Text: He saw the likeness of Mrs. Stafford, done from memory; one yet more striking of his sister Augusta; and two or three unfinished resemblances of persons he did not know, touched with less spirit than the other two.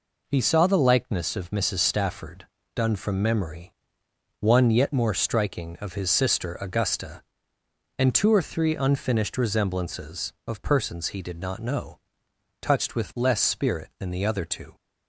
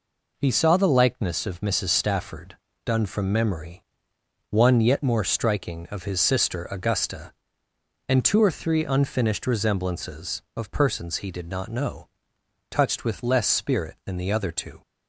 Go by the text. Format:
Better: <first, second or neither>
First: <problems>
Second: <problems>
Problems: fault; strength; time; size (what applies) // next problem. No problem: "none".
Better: neither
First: none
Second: none